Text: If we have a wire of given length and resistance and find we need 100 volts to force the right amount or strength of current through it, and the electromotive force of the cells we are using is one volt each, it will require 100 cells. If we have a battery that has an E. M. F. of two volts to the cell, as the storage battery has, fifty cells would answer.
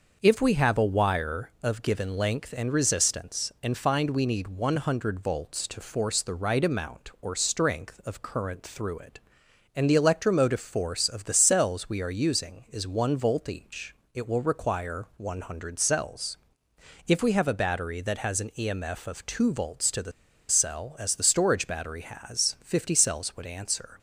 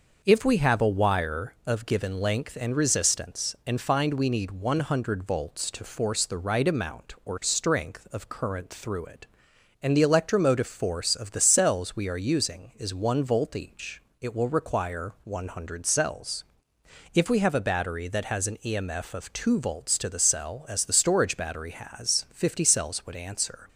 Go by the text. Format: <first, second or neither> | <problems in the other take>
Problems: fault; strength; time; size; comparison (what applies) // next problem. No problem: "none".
second | starts louder than the rest; until 1.2 s; 6 dB; also in the second // pauses between "the" and "cell"; at 20.1 s; 0.38 s long